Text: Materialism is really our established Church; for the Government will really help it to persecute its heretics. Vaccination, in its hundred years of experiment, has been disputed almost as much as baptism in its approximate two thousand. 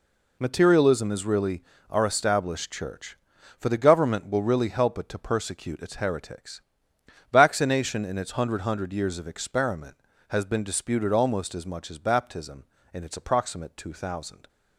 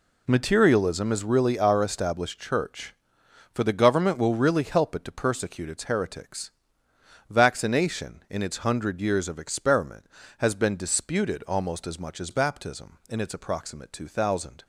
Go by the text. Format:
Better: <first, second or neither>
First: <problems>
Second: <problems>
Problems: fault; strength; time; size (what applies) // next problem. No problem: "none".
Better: second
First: pauses between "really" and "our"; slight; at 1.6 s; 0.28 s long // says "hundred" twice; at 8.6 s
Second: none